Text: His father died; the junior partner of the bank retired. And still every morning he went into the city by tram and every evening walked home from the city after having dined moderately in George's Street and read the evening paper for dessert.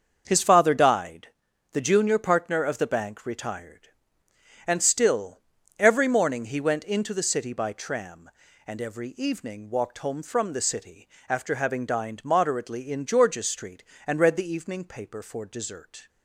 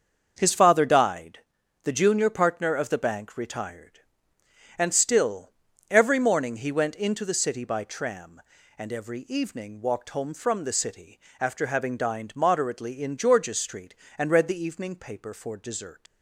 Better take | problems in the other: first | starts louder than the rest; until 1.3 s; 7 dB; also in the first // pauses between "still" and "every"; at 5.4 s; 0.40 s long; also in the first // pauses between "city" and "after"; slight; at 11.1 s; 0.22 s long; slight in the first // leaves "dessert" unfinished; at 16.0 s; 135 ms

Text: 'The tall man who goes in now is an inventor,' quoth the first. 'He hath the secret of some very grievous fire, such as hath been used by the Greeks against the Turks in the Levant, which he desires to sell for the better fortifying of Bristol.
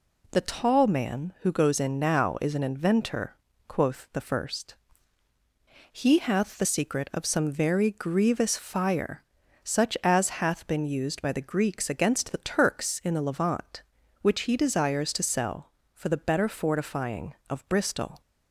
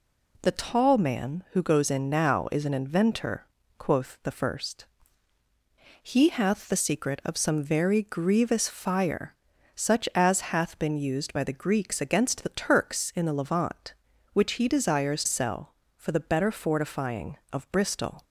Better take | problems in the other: first | skips "to"; at 15.2 s

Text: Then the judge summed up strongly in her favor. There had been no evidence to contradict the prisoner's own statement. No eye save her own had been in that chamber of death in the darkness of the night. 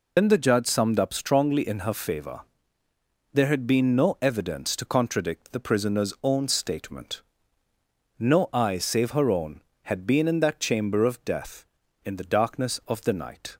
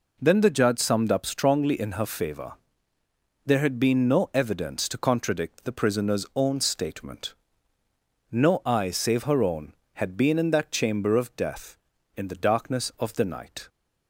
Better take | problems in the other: second | loses the start of "Then"; at 0.1 s; 95 ms

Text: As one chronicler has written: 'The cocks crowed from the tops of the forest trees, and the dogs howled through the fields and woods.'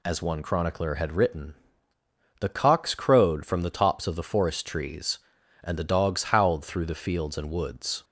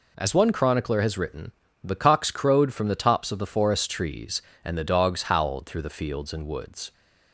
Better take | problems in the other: second | says "had" for "has"; at 0.9 s

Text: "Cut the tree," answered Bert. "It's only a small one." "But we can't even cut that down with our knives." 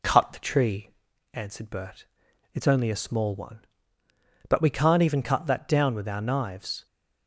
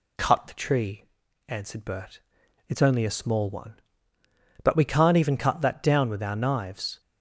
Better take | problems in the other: second | starts louder than the rest; slight; until 1.3 s; 2.5 dB

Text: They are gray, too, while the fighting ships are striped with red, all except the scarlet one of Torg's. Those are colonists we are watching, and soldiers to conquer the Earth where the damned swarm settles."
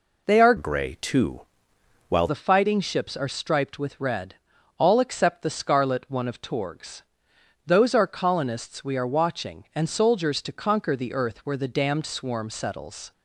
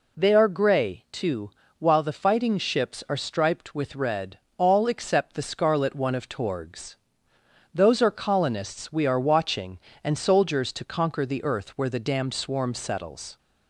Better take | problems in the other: second | changes voice from "gray" to "while"; from 0.5 to 2.2 s; 1.7 s long

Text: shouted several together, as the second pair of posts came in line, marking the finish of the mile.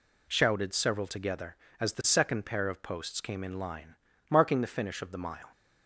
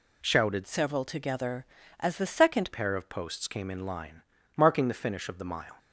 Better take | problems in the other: first | changes voice from "several" to "second"; from 0.6 to 2.7 s; 2.1 s long

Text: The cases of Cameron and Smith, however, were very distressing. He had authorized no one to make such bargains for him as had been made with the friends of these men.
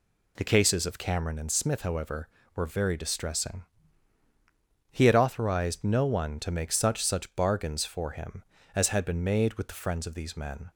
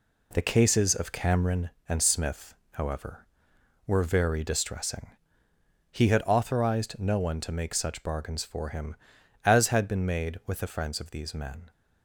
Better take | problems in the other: second | says "such" twice; at 7.0 s

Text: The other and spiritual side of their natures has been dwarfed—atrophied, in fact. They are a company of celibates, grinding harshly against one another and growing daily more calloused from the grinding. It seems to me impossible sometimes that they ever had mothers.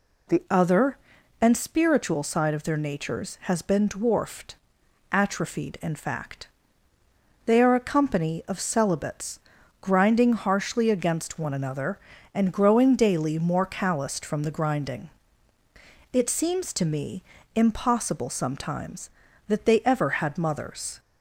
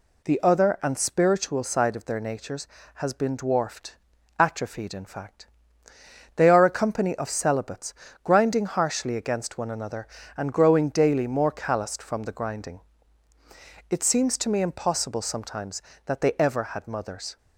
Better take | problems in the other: second | changes voice at "other"; from 0.4 s on; 20.5 s long // pauses between "me" and "impossible"; slight; at 17.2 s; 0.32 s long

